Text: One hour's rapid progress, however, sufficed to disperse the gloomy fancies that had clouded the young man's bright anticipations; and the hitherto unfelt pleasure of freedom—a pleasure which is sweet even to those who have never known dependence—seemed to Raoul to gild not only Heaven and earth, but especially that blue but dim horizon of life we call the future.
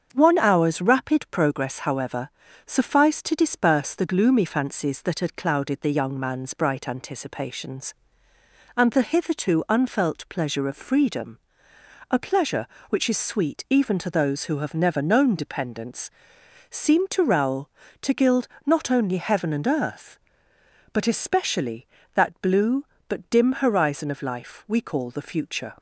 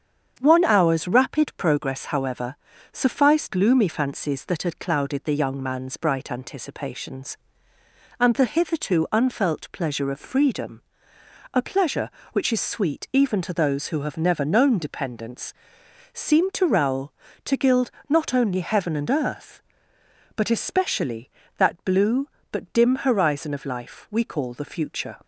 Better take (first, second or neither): first